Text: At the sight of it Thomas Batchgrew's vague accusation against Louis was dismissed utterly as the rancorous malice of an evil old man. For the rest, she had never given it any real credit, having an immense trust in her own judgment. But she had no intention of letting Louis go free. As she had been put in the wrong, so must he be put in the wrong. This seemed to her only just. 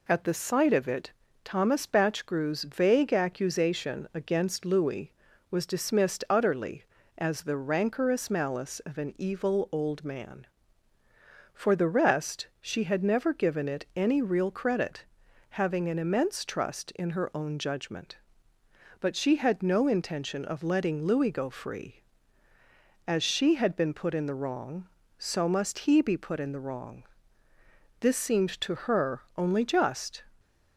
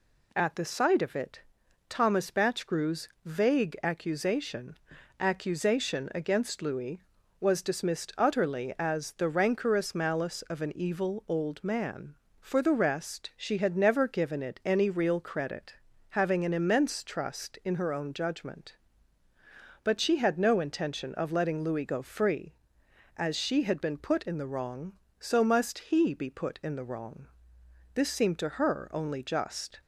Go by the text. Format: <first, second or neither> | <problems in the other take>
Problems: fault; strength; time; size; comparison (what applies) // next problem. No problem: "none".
first | pauses between "it" and "Thomas"; noticeable; at 1.4 s; 0.48 s long; slight in the first // pauses between "Batchgrew's" and "vague"; slight; at 3.0 s; 0.16 s long // says "accusation" twice; at 5.1 s